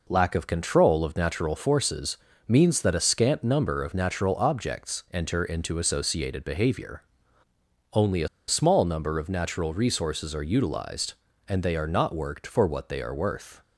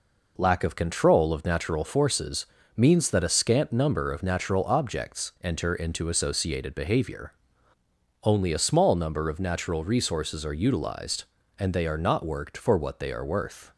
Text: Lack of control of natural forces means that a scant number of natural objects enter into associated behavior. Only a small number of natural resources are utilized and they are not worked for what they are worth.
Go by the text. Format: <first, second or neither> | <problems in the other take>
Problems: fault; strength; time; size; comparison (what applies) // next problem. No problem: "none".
second | pauses between "forces" and "means"; slight; at 2.1 s; 0.32 s long; slight in the second // pauses between "a" and "small"; slight; at 8.2 s; 0.20 s long